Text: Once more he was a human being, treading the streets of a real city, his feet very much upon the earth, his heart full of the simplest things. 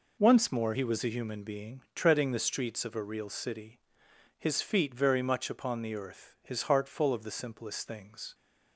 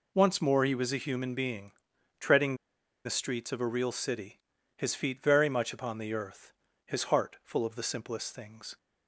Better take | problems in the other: first | pauses between "treading" and "the"; noticeable; at 2.5 s; 0.50 s long

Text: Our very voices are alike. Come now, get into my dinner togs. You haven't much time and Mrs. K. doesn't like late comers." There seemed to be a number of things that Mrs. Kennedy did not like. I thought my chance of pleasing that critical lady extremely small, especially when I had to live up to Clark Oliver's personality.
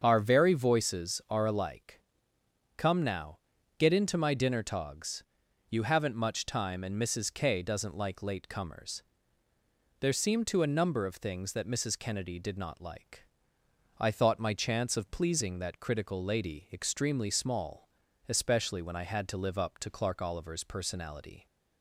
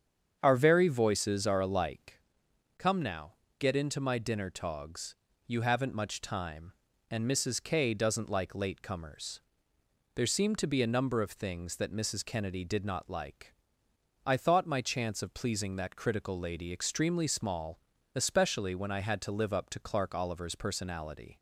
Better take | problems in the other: second | starts louder than the rest; strong; until 1.0 s; 7 dB; strong in the second // skips "be"; at 10.6 s

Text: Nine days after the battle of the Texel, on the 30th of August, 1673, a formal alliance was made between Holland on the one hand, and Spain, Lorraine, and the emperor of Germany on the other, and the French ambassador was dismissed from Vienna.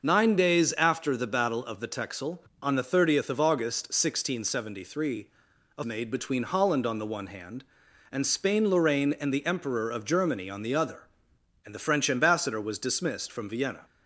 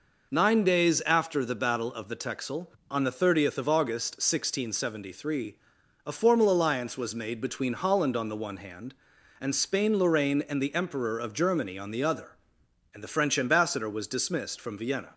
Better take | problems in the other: second | starts louder than the rest; noticeable; until 1.0 s; 6 dB // skips "formal alliance was"; at 5.8 s

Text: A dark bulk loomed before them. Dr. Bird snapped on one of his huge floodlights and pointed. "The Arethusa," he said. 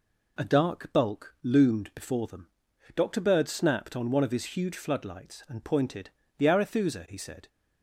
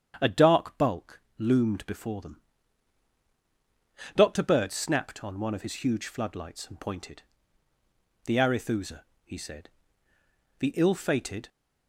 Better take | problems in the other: first | starts louder than the rest; strong; until 1.2 s; 8.5 dB // pauses between "bulk" and "loomed"; slight; at 1.2 s; 0.18 s long // goes on to say "The ill fated"; noticeable; from 10.5 s on; 0.90 s long

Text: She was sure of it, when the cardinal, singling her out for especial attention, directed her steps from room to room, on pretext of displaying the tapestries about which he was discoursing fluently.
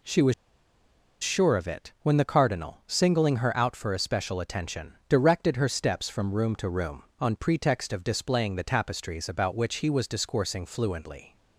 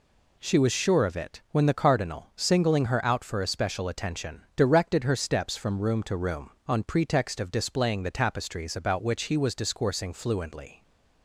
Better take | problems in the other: second | pauses between "was" and "sure"; noticeable; at 0.3 s; 0.89 s long

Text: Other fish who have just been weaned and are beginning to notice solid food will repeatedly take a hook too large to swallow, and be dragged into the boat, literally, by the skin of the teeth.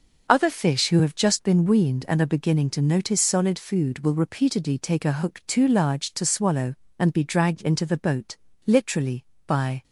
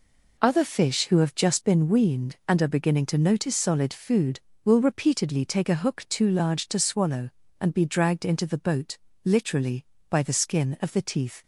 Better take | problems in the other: second | stops before "the skin of the teeth"; at 9.8 s

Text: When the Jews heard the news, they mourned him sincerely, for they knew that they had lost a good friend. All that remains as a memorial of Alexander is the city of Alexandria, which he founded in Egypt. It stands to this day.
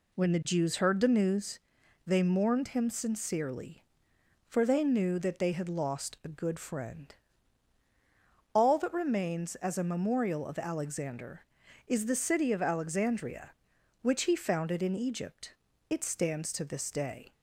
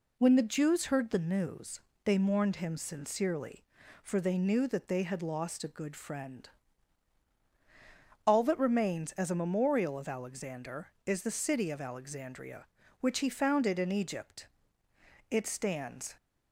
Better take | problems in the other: first | stops before "to this day"; at 16.1 s

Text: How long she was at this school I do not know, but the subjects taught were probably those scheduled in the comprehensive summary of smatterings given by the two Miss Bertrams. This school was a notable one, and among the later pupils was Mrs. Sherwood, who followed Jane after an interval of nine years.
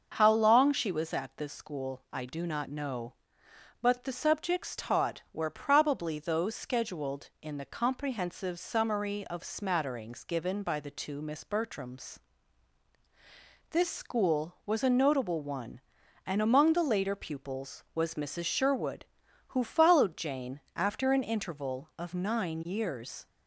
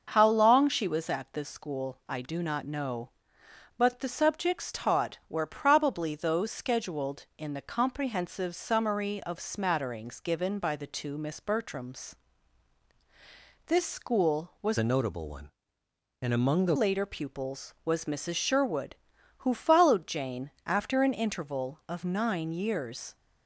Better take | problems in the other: first | starts louder than the rest; until 1.1 s; 6.5 dB; also in the first // changes voice from "a" to "the"; from 14.7 to 16.7 s; 2.0 s long // pauses between "Jane" and "after"; slight; at 20.5 s; 0.16 s long; slight in the first

